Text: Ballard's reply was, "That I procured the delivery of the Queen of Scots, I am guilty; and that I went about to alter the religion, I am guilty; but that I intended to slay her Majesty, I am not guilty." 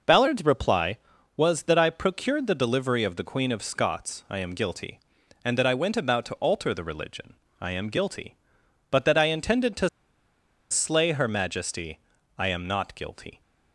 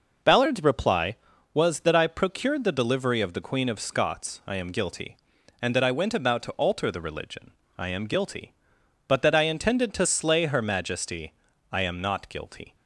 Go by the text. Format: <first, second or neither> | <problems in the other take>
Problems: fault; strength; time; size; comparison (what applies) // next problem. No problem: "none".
second | pauses between "to" and "slay"; noticeable; at 9.8 s; 0.83 s long